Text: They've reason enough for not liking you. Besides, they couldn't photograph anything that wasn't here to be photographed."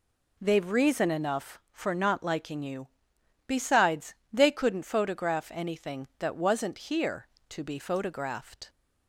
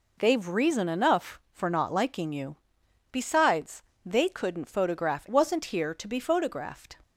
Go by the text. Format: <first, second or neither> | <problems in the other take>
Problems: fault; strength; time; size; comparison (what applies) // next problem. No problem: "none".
first | skips "anything that"; at 5.2 s